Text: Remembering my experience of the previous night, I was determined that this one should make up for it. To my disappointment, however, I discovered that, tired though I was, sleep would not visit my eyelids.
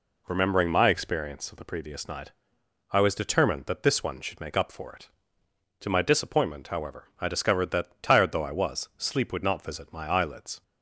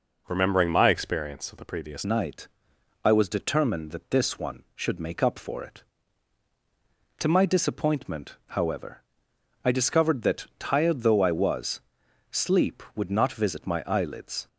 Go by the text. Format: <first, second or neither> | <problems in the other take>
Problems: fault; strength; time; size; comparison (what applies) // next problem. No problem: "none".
first | changes voice at "night"; from 2.0 s on; 12.4 s long